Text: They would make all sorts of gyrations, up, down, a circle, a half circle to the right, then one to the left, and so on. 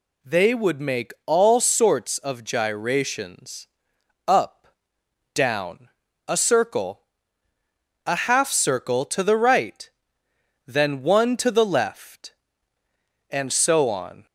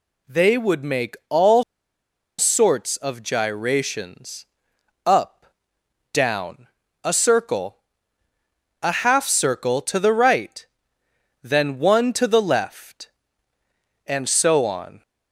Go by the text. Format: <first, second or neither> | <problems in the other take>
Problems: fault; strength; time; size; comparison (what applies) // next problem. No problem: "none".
first | pauses between "all" and "sorts"; noticeable; at 1.6 s; 0.76 s long